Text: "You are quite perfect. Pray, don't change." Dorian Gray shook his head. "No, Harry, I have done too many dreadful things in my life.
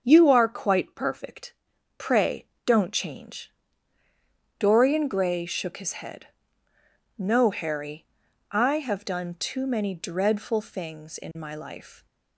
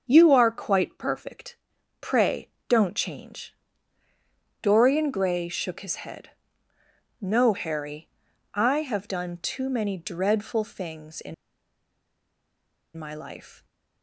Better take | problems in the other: first | starts louder than the rest; until 1.1 s; 7 dB; also in the first // pauses between "in" and "my"; strong; at 11.3 s; 1.6 s long

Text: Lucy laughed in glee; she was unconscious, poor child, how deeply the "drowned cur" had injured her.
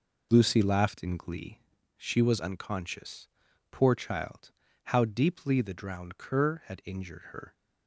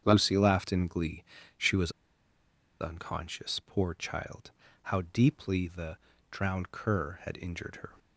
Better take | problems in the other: first | starts louder than the rest; strong; until 1.0 s; 8 dB // pauses between "was" and "unconscious"; noticeable; at 1.8 s; 0.90 s long // pauses between "the" and "drowned"; slight; at 5.9 s; 0.34 s long

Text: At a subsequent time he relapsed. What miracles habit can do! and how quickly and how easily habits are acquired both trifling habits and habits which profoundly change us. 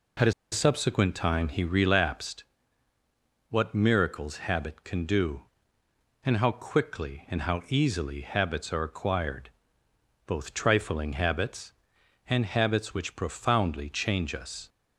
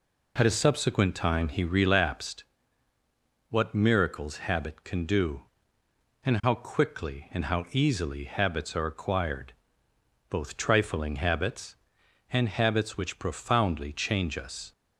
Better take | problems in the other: second | pauses between "a" and "subsequent"; slight; at 0.3 s; 0.19 s long // pauses between "acquired" and "both"; noticeable; at 9.4 s; 0.78 s long; noticeable in the second

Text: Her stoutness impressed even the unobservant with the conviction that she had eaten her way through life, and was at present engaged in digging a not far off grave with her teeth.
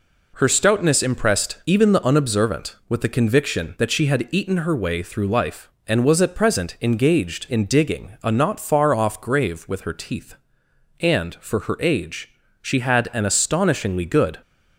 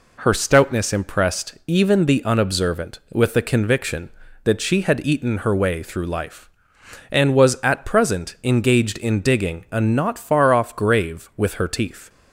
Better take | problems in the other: second | goes on to say "And for her age she had an astonishingly good"; strong; from 10.9 s on; 3.4 s long

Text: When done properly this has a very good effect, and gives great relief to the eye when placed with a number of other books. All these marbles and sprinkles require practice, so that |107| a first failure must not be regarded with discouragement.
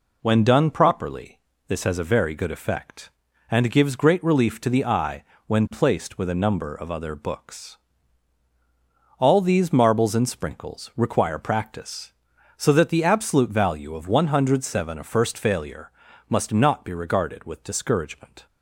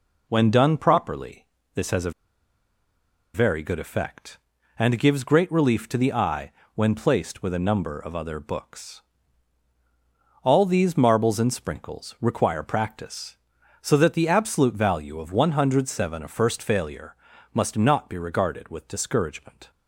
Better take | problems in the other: first | pauses between "properly" and "this"; slight; at 1.4 s; 0.30 s long; slight in the first // pauses between "a" and "very"; at 2.1 s; 1.2 s long // pauses between "eye" and "when"; slight; at 6.5 s; 0.24 s long; slight in the first // pauses between "failure" and "must"; slight; at 17.1 s; 0.36 s long; slight in the first

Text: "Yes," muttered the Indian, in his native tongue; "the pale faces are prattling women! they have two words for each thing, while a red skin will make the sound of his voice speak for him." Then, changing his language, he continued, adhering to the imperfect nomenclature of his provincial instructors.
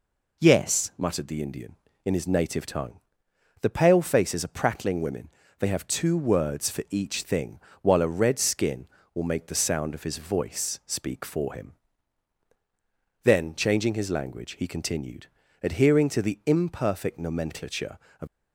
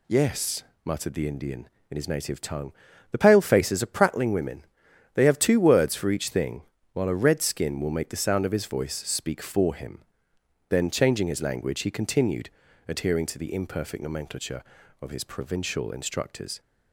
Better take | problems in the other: second | stops before "his provincial instructors"; at 18.2 s

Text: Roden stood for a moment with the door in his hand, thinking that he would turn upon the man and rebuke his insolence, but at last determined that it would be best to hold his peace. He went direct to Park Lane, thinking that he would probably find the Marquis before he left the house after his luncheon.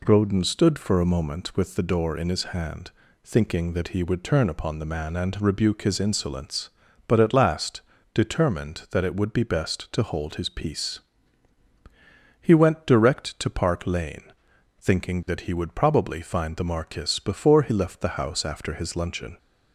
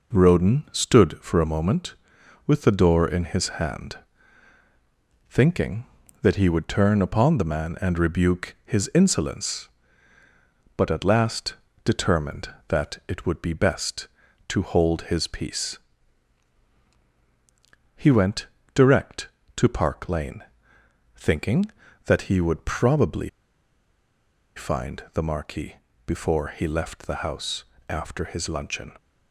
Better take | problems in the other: first | pauses between "last" and "determined"; slight; at 11.5 s; 0.32 s long; slight in the first // pauses between "went" and "direct"; slight; at 18.4 s; 0.26 s long // pauses between "probably" and "find"; strong; at 23.2 s; 1.2 s long // pauses between "Marquis" and "before"; slight; at 25.7 s; 0.32 s long // pauses between "house" and "after"; slight; at 27.6 s; 0.24 s long

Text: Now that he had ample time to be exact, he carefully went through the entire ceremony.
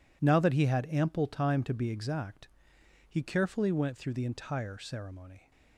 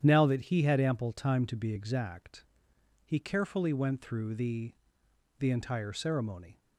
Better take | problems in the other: first | starts louder than the rest; strong; until 1.0 s; 9.5 dB // says "the" twice; at 5.3 s

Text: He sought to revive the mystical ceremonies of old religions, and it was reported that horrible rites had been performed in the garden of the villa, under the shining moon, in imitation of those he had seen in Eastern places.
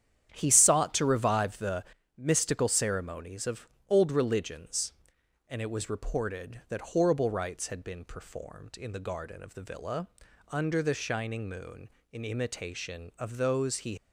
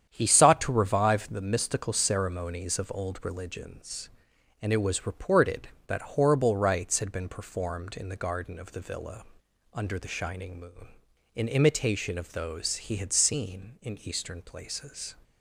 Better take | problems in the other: second | starts louder than the rest; strong; until 1.3 s; 9.5 dB; strong in the second // pauses between "the" and "mystical"; slight; at 1.8 s; 0.32 s long // pauses between "of" and "old"; slight; at 3.6 s; 0.20 s long // stops before "had seen in Eastern places"; at 13.9 s

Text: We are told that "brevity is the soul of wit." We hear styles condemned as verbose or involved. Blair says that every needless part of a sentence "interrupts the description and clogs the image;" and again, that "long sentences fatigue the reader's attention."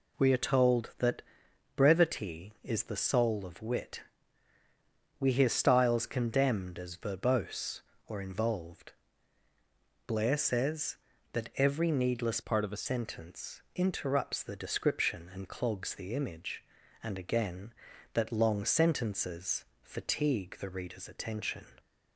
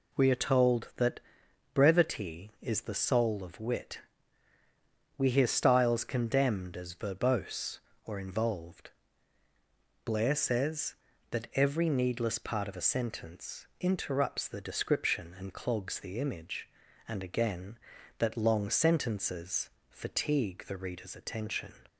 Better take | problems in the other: second | pauses between "that" and "brevity"; noticeable; at 1.2 s; 0.52 s long; noticeable in the second // changes voice from "part" to "a"; from 12.4 to 12.8 s; 0.4 s long // pauses between "sentences" and "fatigue"; slight; at 19.6 s; 0.18 s long; slight in the second

